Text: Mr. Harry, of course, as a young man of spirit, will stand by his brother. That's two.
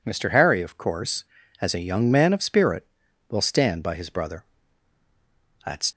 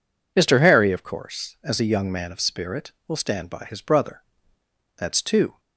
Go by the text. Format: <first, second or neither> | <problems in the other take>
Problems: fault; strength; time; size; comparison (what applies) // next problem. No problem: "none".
second | stops before "two"; at 5.9 s